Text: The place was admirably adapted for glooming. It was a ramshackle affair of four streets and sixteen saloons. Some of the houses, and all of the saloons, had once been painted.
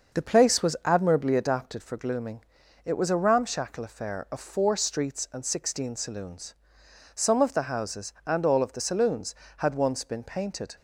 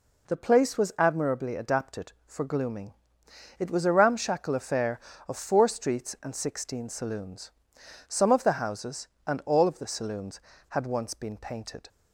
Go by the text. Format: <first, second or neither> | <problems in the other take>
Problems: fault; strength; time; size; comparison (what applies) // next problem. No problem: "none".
second | starts louder than the rest; until 1.9 s; 6 dB